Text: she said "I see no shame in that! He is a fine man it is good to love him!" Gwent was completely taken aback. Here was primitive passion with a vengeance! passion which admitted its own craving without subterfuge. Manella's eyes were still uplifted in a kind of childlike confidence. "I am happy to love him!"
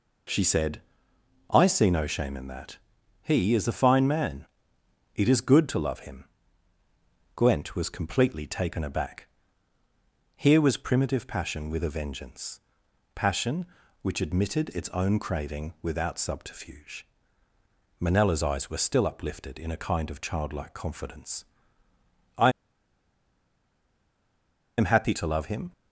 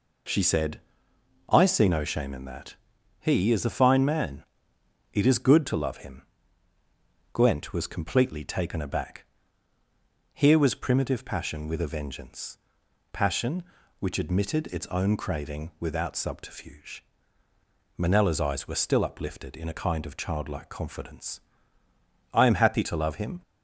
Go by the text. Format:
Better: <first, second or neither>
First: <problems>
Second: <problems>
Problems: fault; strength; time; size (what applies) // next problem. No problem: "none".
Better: second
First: pauses between "said" and "I"; noticeable; at 0.8 s; 0.68 s long // pauses between "man" and "it"; noticeable; at 4.4 s; 0.68 s long // pauses between "I" and "am"; strong; at 22.5 s; 2.2 s long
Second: pauses between "said" and "I"; noticeable; at 0.8 s; 0.68 s long // pauses between "man" and "it"; noticeable; at 4.4 s; 0.68 s long